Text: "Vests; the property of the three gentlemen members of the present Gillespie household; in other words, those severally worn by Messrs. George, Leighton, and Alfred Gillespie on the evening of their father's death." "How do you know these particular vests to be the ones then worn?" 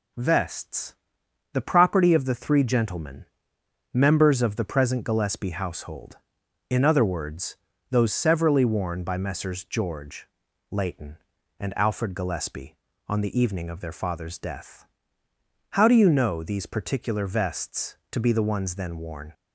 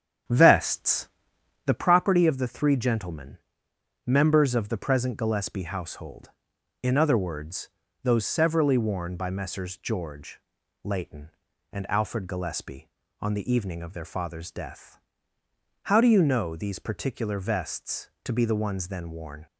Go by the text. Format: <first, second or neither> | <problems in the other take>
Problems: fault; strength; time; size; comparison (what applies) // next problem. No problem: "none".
first | starts louder than the rest; strong; until 1.9 s; 8.5 dB // pauses between "gentlemen" and "members"; noticeable; at 3.3 s; 0.66 s long; noticeable in the first